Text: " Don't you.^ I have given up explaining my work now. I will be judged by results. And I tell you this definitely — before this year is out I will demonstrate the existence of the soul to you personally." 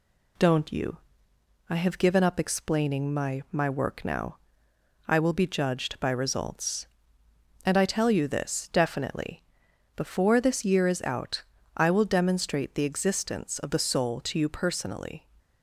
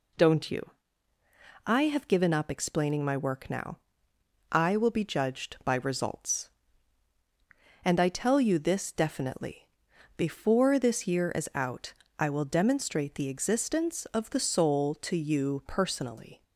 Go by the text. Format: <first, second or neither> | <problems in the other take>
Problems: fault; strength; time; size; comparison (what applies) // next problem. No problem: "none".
second | says "my" twice; at 3.5 s // pauses between "out" and "I"; slight; at 11.4 s; 0.32 s long; slight in the second